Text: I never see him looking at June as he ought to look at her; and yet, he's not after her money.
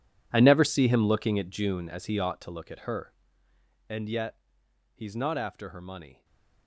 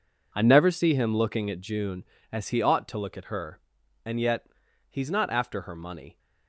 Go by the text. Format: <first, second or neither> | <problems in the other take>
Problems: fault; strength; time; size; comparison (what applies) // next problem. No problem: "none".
second | gets quieter; strong; throughout; 17.5 dB // stays silent after the last word; slight; from 6.1 s on; 0.5 s long